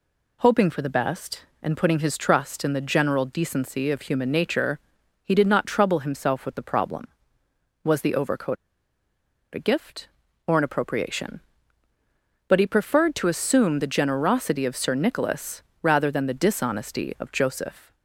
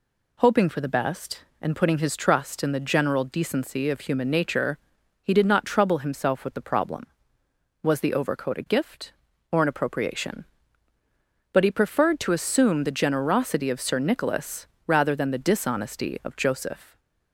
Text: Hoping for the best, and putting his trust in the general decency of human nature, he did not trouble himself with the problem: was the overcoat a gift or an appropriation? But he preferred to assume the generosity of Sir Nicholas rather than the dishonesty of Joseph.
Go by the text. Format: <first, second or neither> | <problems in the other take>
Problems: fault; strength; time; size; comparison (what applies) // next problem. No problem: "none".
second | pauses between "overcoat" and "a"; at 8.5 s; 0.98 s long // pauses between "Nicholas" and "rather"; slight; at 15.6 s; 0.18 s long; slight in the second